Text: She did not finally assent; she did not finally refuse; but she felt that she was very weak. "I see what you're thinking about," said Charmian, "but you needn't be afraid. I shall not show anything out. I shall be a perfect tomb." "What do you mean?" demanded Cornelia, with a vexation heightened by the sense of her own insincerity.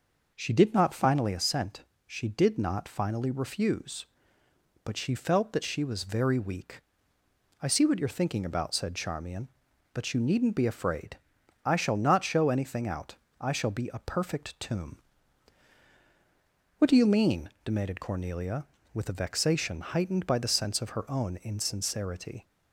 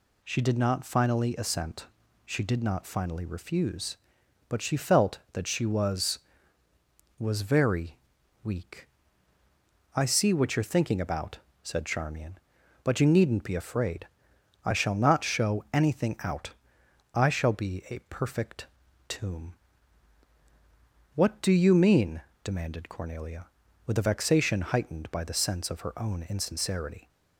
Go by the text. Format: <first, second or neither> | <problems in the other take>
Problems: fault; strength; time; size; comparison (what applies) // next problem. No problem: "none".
first | says "was" twice; at 7.1 s // pauses between "very" and "weak"; noticeable; at 7.9 s; 0.48 s long // pauses between "perfect" and "tomb"; at 18.6 s; 0.42 s long